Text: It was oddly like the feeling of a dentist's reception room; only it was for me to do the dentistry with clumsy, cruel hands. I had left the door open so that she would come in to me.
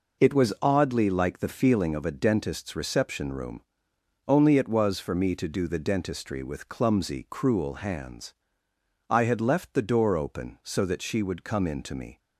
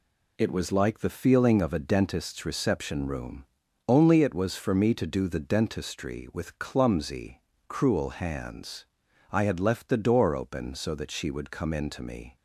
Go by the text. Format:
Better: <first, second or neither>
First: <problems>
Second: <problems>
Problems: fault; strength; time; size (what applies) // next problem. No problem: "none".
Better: first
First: none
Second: skips "oddly"; at 0.7 s